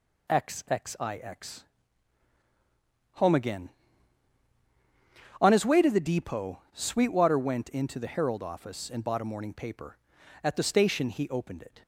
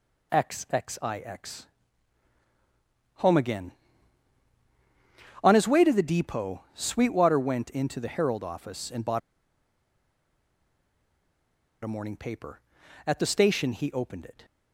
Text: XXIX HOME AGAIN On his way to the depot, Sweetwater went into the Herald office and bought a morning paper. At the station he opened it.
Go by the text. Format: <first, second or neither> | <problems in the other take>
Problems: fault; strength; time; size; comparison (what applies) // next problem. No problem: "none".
first | pauses between "XXIX" and "HOME"; strong; at 1.6 s; 1.5 s long; strong in the first // pauses between "bought" and "a"; strong; at 9.2 s; 2.6 s long